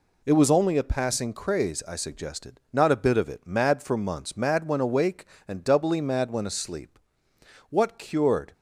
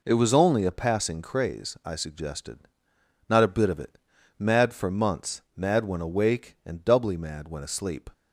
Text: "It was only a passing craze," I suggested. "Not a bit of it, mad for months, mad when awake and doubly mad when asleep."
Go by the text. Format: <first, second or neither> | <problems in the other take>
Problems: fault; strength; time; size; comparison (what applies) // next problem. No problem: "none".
second | goes on to say "What cured"; noticeable; from 7.7 s on; 0.82 s long